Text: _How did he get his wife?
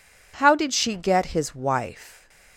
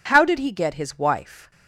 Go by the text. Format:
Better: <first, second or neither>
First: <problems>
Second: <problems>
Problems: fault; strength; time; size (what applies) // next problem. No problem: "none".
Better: second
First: says "she" for "he"; at 0.7 s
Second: none